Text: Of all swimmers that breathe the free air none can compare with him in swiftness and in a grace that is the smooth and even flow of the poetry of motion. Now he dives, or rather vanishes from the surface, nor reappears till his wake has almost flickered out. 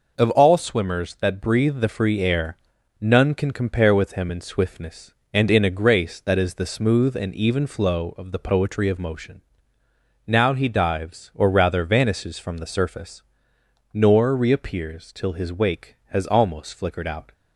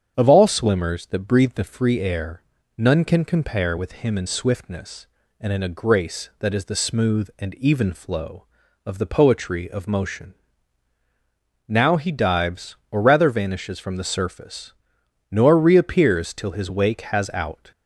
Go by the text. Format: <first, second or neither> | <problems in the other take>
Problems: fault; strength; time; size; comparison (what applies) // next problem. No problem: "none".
first | starts louder than the rest; strong; until 1.1 s; 7.5 dB // pauses between "air" and "none"; slight; at 2.4 s; 0.36 s long; noticeable in the first // skips "almost flickered"; at 17.3 s